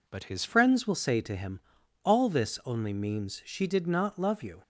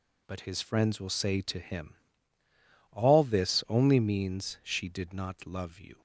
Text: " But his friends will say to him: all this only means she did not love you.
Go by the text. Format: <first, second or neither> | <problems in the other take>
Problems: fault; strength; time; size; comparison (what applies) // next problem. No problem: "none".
second | changes voice at "friends"; from 0.4 s on; 4.2 s long